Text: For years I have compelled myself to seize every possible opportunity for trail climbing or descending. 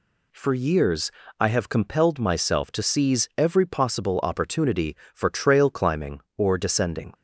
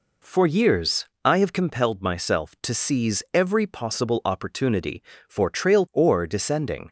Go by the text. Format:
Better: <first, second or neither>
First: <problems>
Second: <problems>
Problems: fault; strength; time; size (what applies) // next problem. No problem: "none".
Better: first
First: pauses between "years" and "I"; slight; at 1.1 s; 0.28 s long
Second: pauses between "years" and "I"; slight; at 1.0 s; 0.20 s long // skips "climbing"; at 5.8 s